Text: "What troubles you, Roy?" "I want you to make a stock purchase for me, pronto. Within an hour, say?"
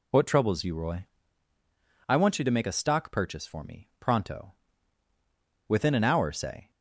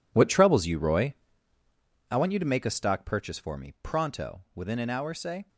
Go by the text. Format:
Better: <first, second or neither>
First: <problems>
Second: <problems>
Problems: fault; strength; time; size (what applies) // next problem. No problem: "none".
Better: first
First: none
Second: gets quieter; strong; throughout; 13.5 dB